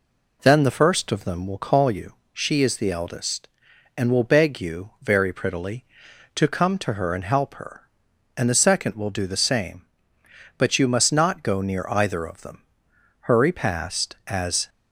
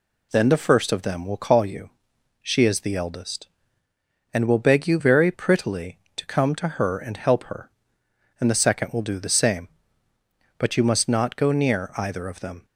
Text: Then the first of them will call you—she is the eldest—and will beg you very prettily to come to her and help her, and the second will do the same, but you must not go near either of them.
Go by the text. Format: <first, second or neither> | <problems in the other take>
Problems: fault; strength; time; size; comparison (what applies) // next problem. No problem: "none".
second | goes on to say "Hurry past as"; from 13.2 s on; 1.4 s long